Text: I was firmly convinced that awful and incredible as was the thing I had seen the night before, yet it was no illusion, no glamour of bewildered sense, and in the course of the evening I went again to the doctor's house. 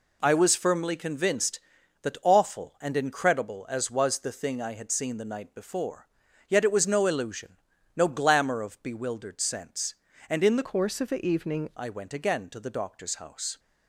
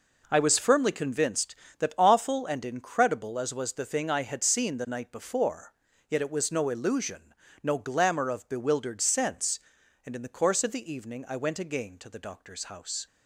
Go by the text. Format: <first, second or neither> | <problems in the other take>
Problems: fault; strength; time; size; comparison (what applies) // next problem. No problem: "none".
second | changes voice from "course" to "evening"; from 10.6 to 11.7 s; 1.1 s long